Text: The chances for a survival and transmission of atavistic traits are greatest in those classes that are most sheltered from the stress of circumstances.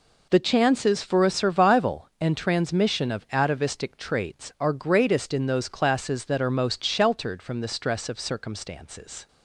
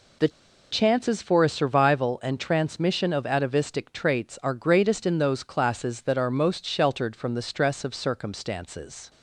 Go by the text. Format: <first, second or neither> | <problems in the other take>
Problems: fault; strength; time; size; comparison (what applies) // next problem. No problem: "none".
first | pauses between "The" and "chances"; at 0.2 s; 0.42 s long